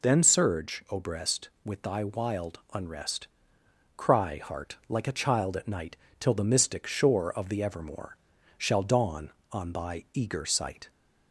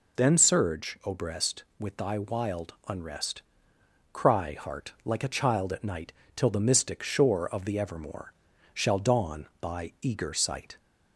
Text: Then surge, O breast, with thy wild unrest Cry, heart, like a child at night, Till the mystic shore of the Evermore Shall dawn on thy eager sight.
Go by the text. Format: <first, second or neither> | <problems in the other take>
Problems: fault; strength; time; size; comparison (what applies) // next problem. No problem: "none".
first | pauses between "unrest" and "Cry"; noticeable; at 3.4 s; 0.70 s long; noticeable in the first // pauses between "Evermore" and "Shall"; at 8.3 s; 0.42 s long; also in the first // skips "on"; at 9.5 s